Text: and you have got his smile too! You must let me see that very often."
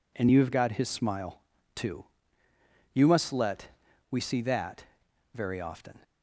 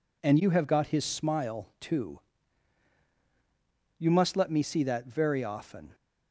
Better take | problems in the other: second | pauses between "smile" and "too"; slight; at 1.3 s; 0.34 s long // says "we" for "me"; at 4.1 s // pauses between "that" and "very"; noticeable; at 4.8 s; 0.48 s long

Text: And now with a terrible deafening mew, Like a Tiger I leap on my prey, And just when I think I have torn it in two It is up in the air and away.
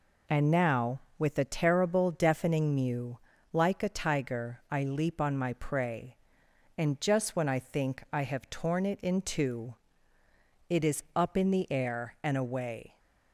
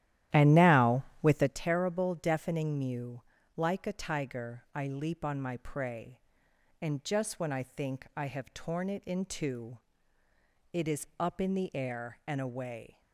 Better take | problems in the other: first | starts louder than the rest; strong; until 1.6 s; 12.5 dB // pauses between "two" and "It"; noticeable; at 9.7 s; 0.94 s long; noticeable in the first

